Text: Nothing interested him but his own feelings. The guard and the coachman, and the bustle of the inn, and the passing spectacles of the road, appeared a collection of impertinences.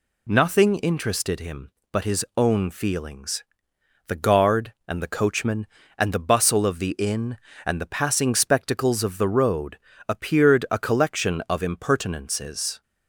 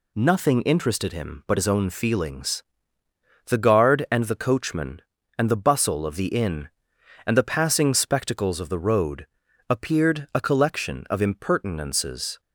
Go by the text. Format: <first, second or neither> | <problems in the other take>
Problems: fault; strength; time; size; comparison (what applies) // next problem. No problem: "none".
neither | none